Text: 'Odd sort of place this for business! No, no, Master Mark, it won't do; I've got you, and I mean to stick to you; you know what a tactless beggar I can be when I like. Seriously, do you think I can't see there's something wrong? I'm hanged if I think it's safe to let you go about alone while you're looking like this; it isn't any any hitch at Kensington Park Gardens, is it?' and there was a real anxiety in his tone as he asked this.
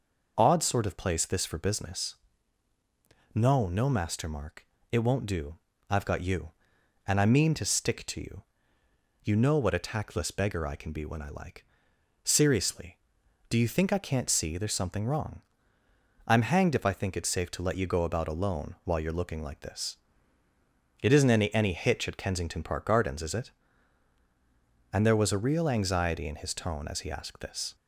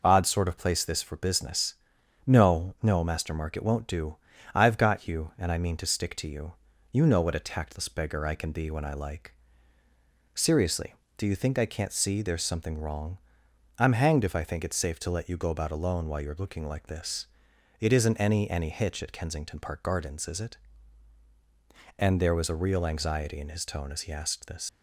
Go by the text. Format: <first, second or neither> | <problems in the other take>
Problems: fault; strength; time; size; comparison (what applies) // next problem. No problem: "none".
first | leaves "this" unfinished; at 24.6 s; 125 ms